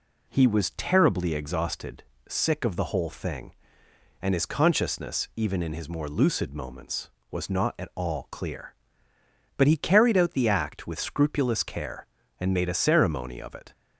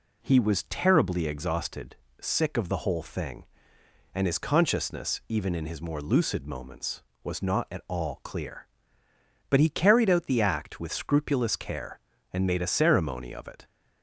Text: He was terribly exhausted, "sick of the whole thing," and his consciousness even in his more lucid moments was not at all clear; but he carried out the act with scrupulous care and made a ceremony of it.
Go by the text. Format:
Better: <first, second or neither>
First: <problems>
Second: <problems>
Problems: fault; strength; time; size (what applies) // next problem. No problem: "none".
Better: neither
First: none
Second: none